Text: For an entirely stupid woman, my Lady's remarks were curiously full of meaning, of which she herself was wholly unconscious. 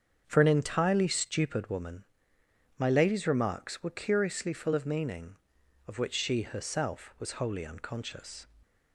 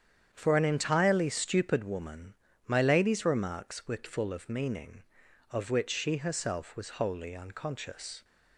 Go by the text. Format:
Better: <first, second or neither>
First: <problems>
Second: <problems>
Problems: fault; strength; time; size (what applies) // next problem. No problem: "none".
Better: first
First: starts louder than the rest; strong; until 1.2 s; 7.5 dB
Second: starts louder than the rest; strong; until 1.3 s; 8.5 dB // skips "curiously"; at 4.0 s